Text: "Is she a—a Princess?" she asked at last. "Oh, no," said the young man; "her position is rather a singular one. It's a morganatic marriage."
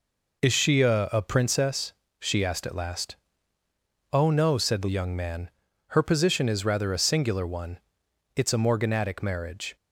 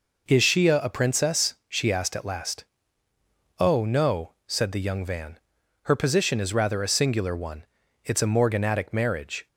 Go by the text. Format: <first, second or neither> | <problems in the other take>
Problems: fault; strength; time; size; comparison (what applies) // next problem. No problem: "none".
first | says "van" for "man"; at 5.0 s